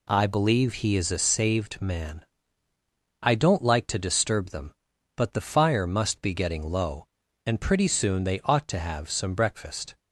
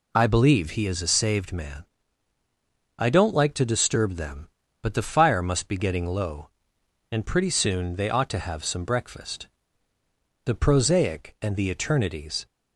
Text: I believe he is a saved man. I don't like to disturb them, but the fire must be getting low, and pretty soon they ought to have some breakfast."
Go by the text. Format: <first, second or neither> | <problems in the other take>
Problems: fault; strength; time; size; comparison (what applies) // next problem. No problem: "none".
first | goes on to say "The prosaic and the eternities"; strong; from 10.4 s on; 2.0 s long